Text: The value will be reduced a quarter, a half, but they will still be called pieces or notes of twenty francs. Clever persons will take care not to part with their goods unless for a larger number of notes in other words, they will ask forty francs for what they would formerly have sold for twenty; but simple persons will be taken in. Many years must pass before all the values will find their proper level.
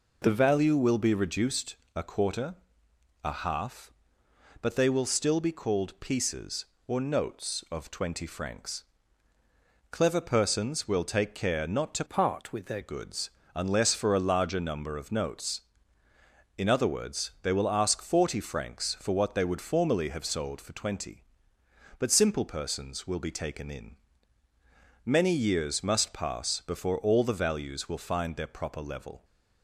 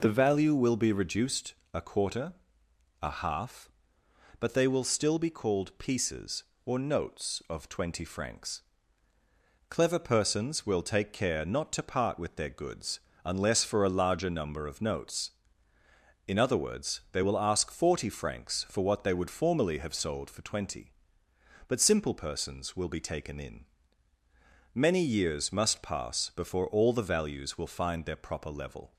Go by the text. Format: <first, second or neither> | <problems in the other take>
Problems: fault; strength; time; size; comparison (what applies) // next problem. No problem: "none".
second | pauses between "reduced" and "a"; slight; at 1.7 s; 0.22 s long; slight in the second // changes voice from "part" to "their"; from 12.0 to 12.8 s; 0.8 s long // pauses between "goods" and "unless"; slight; at 13.3 s; 0.26 s long; slight in the second